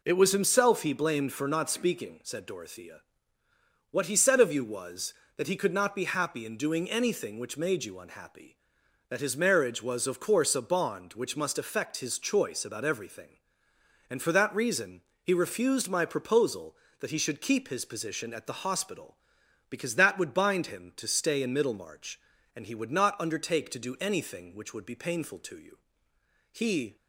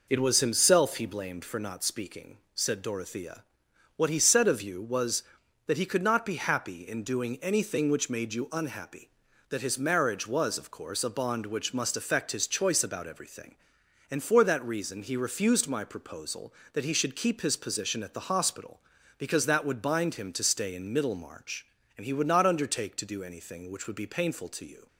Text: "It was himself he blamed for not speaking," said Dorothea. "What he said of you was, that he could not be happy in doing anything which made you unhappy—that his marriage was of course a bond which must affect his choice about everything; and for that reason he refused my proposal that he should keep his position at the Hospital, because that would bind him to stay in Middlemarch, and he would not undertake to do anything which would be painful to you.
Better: second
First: pauses between "reason" and "he"; slight; at 15.0 s; 0.20 s long // goes on to say "He"; slight; from 26.4 s on; 0.46 s long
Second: none

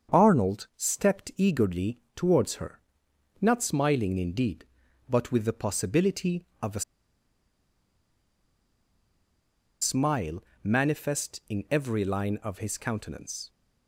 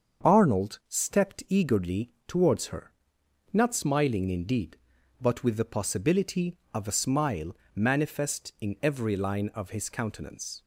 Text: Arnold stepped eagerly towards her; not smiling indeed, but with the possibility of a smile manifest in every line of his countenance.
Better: second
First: starts louder than the rest; strong; until 1.2 s; 7 dB // pauses between "eagerly" and "towards"; slight; at 1.9 s; 0.16 s long // pauses between "a" and "smile"; strong; at 6.8 s; 2.9 s long // pauses between "smile" and "manifest"; slight; at 10.4 s; 0.18 s long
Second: starts louder than the rest; until 1.3 s; 7 dB // pauses between "eagerly" and "towards"; slight; at 2.1 s; 0.16 s long // pauses between "smile" and "manifest"; slight; at 7.5 s; 0.17 s long

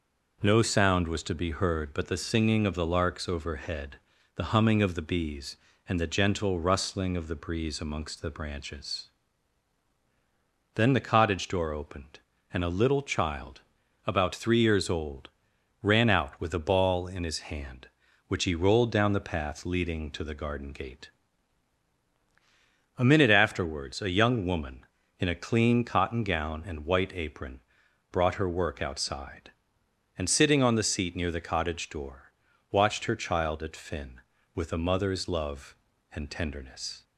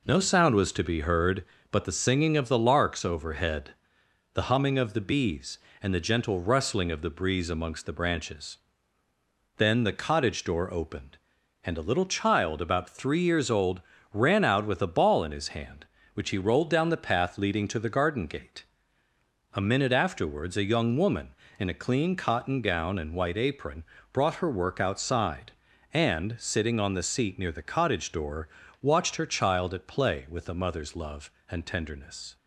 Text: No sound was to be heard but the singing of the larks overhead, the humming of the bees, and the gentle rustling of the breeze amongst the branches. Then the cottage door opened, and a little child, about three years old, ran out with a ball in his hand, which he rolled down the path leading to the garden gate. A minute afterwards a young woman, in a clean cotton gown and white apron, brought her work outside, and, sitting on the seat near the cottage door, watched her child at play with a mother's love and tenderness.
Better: second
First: says "finn" for "play"; at 33.7 s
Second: none

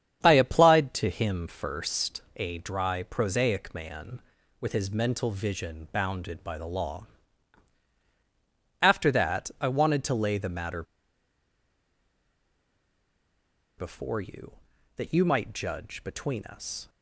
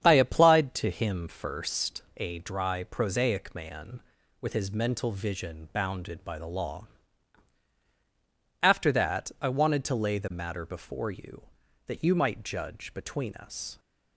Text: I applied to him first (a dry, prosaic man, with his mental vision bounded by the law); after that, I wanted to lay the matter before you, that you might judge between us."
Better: second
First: starts louder than the rest; strong; until 1.2 s; 8.5 dB // pauses between "matter" and "before"; strong; at 10.8 s; 2.9 s long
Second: starts louder than the rest; strong; until 1.0 s; 8.5 dB

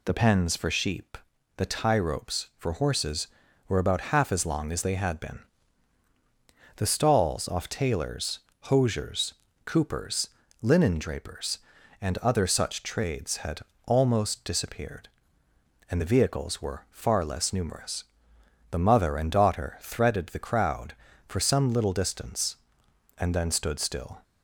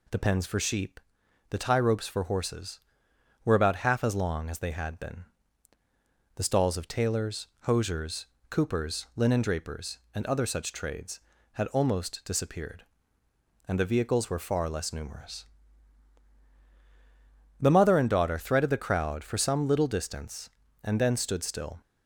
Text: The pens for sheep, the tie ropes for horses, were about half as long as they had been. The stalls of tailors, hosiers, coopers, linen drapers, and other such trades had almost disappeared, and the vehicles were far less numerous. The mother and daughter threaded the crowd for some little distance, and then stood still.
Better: second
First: says "off" for "of"; at 7.4 s // pauses between "had" and "almost"; slight; at 13.6 s; 0.24 s long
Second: none

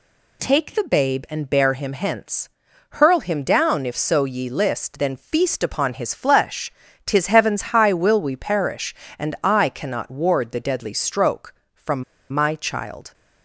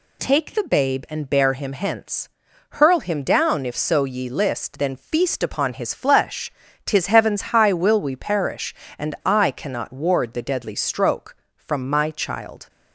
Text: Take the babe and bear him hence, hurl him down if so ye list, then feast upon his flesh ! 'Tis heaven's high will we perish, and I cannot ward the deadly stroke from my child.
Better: second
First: pauses between "heaven's" and "high"; slight; at 7.6 s; 0.16 s long // pauses between "from" and "my"; slight; at 12.0 s; 0.29 s long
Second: pauses between "heaven's" and "high"; slight; at 7.4 s; 0.16 s long

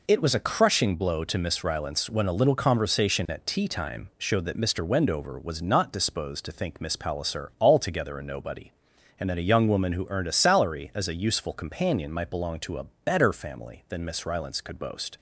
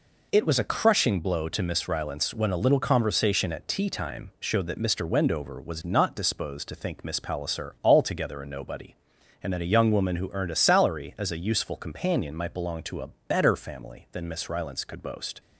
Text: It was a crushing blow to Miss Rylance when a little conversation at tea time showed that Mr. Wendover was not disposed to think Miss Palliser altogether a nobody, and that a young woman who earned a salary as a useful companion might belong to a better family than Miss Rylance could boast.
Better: neither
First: pauses between "a" and "better"; slight; at 12.8 s; 0.20 s long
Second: pauses between "a" and "better"; slight; at 13.0 s; 0.20 s long

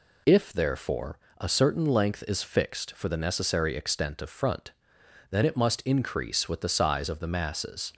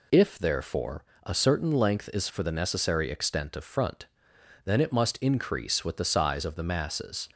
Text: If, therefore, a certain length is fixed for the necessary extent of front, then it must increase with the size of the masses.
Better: first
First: none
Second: skips "fixed"; at 2.2 s

